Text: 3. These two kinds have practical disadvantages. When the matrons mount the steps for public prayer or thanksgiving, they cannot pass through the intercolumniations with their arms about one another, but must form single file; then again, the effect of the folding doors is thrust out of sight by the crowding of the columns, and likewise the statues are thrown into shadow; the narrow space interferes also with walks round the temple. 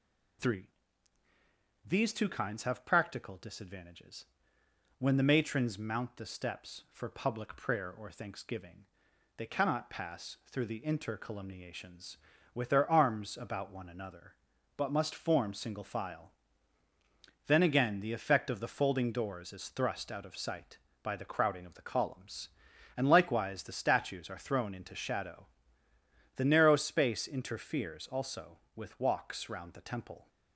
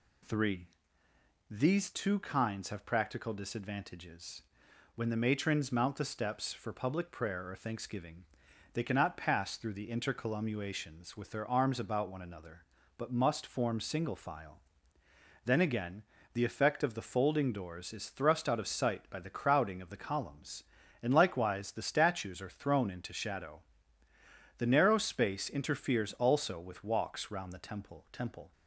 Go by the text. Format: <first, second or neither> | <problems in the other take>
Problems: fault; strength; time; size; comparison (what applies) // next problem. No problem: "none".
first | says "temple" twice; at 28.1 s